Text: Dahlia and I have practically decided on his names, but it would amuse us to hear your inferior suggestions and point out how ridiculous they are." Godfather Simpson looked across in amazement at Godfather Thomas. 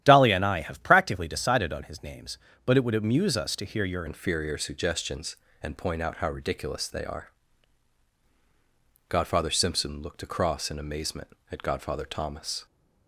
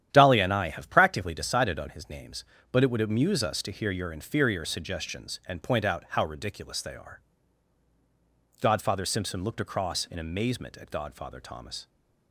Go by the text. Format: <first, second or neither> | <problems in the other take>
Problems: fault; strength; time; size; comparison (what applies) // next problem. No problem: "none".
second | starts louder than the rest; strong; until 1.0 s; 11.5 dB; strong in the second // changes voice at "inferior"; from 4.0 s on; 8.6 s long